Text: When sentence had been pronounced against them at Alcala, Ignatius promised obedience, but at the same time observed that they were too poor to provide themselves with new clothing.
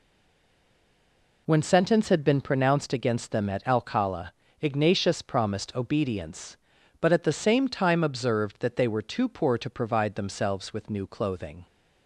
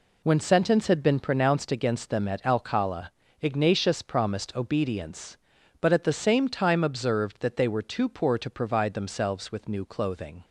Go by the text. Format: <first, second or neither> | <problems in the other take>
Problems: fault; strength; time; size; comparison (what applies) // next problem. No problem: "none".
second | stays silent before the first word; noticeable; until 1.4 s; 1.4 s long